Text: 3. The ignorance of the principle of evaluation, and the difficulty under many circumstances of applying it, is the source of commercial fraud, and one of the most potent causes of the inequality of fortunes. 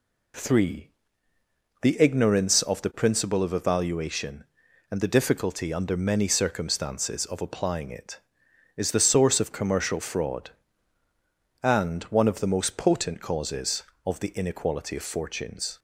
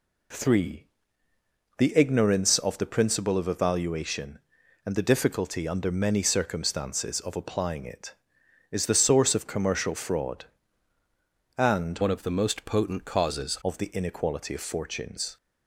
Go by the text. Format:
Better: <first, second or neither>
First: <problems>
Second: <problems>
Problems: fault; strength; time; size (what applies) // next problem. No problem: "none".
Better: first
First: none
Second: changes voice from "one" to "causes"; from 12.0 to 13.5 s; 1.5 s long